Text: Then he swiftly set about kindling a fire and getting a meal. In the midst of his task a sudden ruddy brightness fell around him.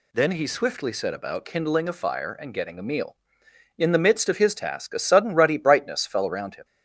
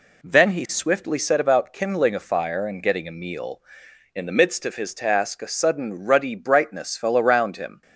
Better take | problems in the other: neither | none

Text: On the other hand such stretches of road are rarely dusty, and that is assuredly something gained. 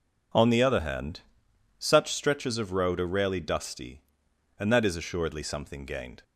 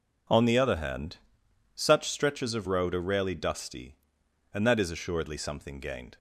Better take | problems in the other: neither | pauses between "hand" and "such"; noticeable; the same in both

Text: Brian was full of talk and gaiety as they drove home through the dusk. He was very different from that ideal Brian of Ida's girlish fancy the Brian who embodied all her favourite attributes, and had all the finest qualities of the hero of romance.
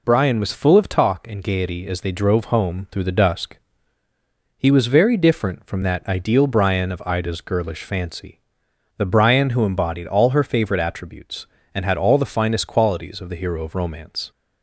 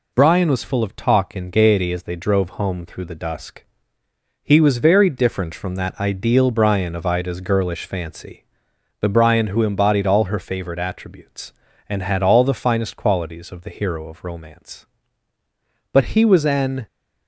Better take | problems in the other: first | pauses between "fancy" and "the"; noticeable; at 8.4 s; 0.56 s long; noticeable in the first // goes on to say "But he was an"; noticeable; from 15.9 s on; 0.94 s long

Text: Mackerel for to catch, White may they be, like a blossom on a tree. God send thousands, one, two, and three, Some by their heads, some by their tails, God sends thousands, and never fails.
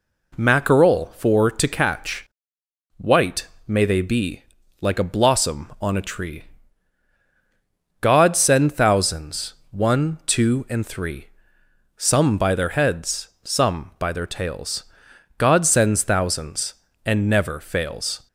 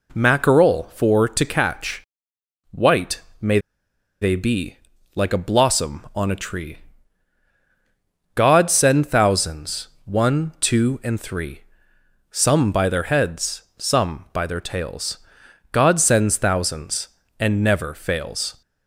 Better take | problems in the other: first | pauses between "White" and "may"; slight; at 3.2 s; 0.20 s long; slight in the first // pauses between "may" and "they"; noticeable; at 3.5 s; 0.62 s long

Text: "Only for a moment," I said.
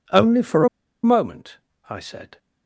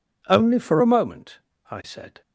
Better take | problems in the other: second | pauses between "a" and "moment"; slight; at 0.6 s; 0.35 s long

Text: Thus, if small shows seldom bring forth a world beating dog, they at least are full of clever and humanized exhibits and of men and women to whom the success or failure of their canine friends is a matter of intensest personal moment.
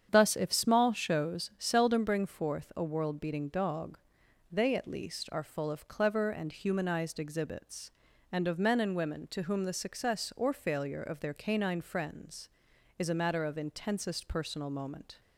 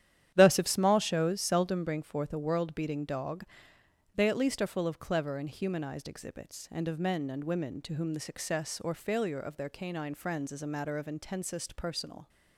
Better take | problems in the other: first | starts louder than the rest; strong; until 1.3 s; 10.5 dB; strong in the first // stops before "moment"; at 12.2 s

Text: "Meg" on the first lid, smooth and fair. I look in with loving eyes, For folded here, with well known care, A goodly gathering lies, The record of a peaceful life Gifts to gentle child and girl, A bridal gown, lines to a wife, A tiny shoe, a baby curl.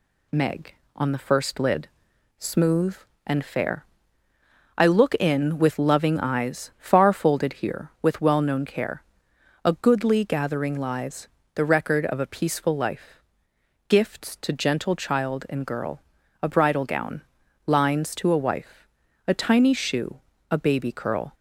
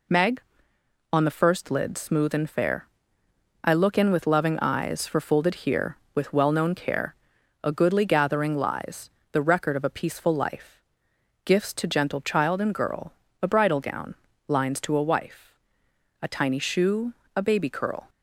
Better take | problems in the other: second | says "Far" for "For"; at 6.7 s // pauses between "life" and "Gifts"; noticeable; at 13.2 s; 0.66 s long; noticeable in the second

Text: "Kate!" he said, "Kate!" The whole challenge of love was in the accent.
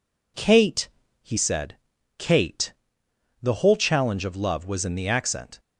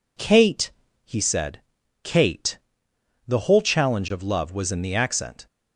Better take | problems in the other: neither | none

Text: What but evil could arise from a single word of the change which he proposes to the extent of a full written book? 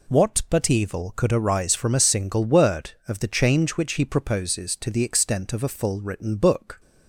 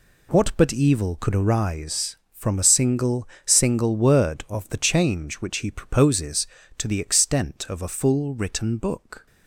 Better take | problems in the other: first | says "single" twice; at 3.4 s

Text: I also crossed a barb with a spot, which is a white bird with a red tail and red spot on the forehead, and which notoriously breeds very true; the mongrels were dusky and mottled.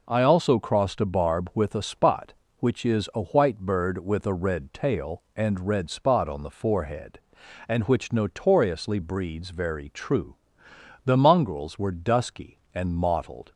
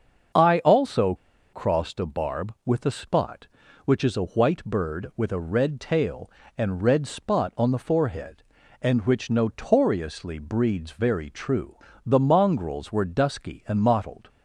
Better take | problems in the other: first | starts louder than the rest; until 1.7 s; 7 dB // pauses between "also" and "crossed"; at 1.1 s; 0.38 s long

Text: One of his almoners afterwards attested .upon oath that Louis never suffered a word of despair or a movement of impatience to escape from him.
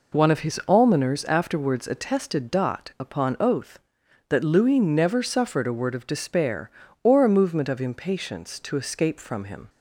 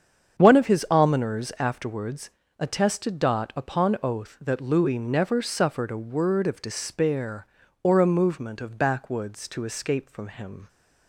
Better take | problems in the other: first | starts louder than the rest; strong; until 1.4 s; 7.5 dB // pauses between "afterwards" and "attested"; slight; at 2.2 s; 0.30 s long // says "backwoods" for "impatience"; at 8.7 s

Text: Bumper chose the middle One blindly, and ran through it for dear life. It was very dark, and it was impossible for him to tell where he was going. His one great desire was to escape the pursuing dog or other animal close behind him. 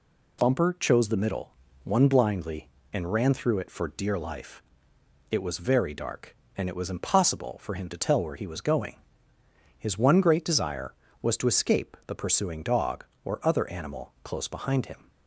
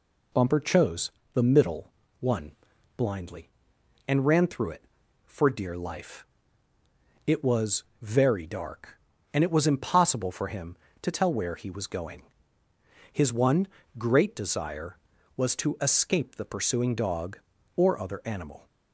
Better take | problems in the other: first | pauses between "chose" and "the"; slight; at 1.1 s; 0.24 s long // pauses between "middle" and "One"; slight; at 1.9 s; 0.28 s long; slight in the first // pauses between "One" and "blindly"; at 2.5 s; 0.44 s long // pauses between "was" and "very"; slight; at 7.8 s; 0.18 s long // pauses between "one" and "great"; slight; at 13.6 s; 0.30 s long // stops before "close behind him"; at 18.6 s

